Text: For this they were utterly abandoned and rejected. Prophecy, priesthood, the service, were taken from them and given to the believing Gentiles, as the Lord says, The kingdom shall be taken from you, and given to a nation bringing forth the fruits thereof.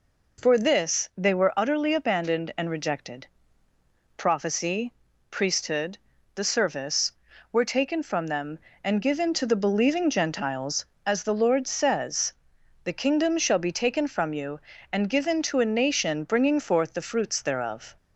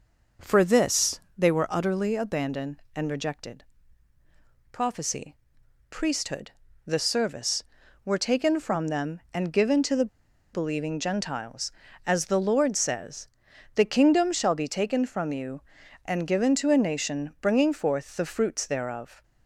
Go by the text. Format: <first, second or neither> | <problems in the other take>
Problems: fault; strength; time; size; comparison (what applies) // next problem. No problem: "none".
first | pauses between "this" and "they"; slight; at 1.2 s; 0.16 s long // pauses between "the" and "believing"; noticeable; at 10.0 s; 0.47 s long